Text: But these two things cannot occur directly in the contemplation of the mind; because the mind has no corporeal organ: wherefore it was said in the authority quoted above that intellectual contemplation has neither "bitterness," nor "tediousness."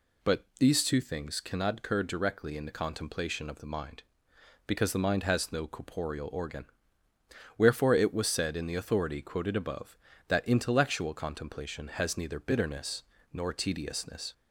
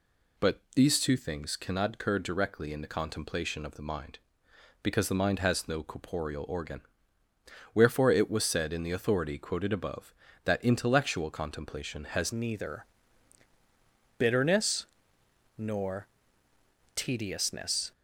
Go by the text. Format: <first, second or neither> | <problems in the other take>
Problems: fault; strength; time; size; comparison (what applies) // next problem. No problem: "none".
first | changes voice at "neither"; from 12.3 s on; 5.6 s long // pauses between "neither" and "bitterness"; strong; at 12.8 s; 1.3 s long // pauses between "nor" and "tediousness"; noticeable; at 16.0 s; 0.88 s long